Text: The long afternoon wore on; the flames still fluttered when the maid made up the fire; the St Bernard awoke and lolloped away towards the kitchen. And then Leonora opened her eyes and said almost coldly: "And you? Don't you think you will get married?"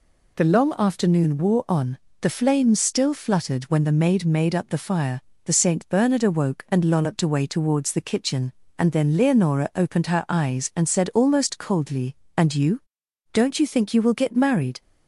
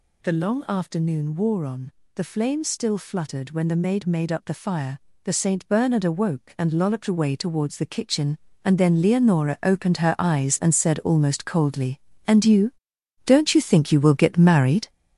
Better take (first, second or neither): first